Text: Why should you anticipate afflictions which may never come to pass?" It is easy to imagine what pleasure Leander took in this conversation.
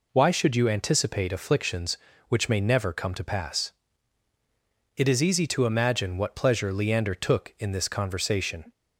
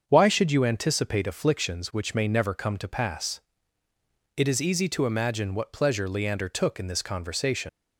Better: first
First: none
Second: starts louder than the rest; until 1.0 s; 7 dB // leaves "conversation" unfinished; at 7.6 s; 120 ms

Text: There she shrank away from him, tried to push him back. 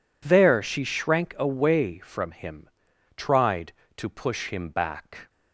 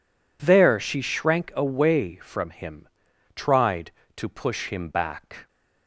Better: neither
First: none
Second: none

